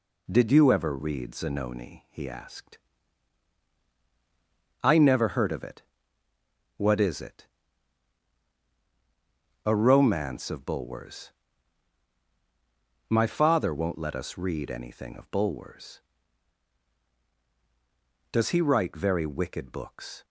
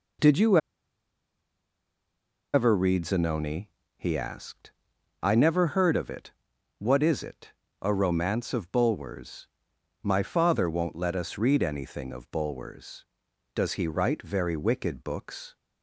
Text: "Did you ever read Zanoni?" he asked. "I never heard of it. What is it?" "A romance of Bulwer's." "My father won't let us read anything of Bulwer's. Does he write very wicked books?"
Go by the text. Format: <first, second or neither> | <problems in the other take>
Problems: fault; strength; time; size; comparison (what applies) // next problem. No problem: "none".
first | pauses between "you" and "ever"; strong; at 0.5 s; 1.9 s long